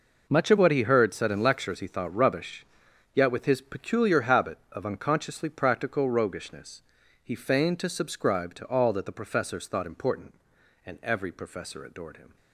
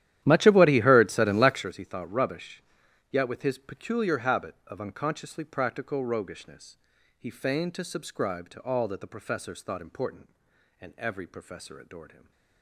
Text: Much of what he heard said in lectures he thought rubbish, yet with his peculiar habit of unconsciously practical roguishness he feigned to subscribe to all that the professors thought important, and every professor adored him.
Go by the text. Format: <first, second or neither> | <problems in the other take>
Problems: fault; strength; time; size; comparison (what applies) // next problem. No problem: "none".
first | starts louder than the rest; strong; until 1.7 s; 12 dB // pauses between "roguishness" and "he"; at 6.7 s; 0.42 s long; also in the first // stays silent after the last word; slight; from 12.0 s on; 0.6 s long